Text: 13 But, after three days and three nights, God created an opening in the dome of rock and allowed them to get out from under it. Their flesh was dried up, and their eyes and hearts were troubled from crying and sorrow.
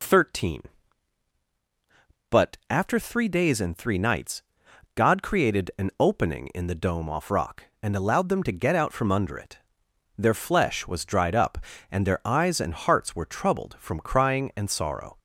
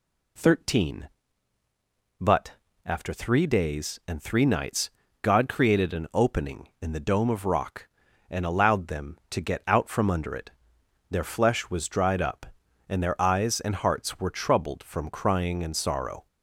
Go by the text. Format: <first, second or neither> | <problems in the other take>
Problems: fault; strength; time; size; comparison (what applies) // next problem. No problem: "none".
second | says "off" for "of"; at 7.0 s